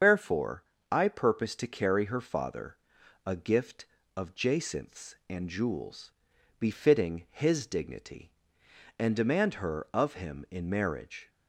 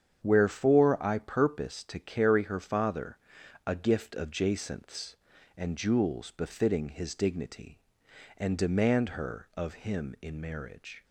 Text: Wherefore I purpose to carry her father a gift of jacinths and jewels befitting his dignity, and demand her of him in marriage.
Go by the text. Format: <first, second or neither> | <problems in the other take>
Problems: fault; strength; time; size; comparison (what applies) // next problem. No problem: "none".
second | loses the start of "Wherefore"; at 0.0 s; 85 ms // starts louder than the rest; strong; until 1.3 s; 7.5 dB; strong in the second // pauses between "Wherefore" and "I"; slight; at 0.6 s; 0.28 s long // pauses between "father" and "a"; noticeable; at 2.7 s; 0.48 s long; noticeable in the second // pauses between "jewels" and "befitting"; noticeable; at 6.1 s; 0.48 s long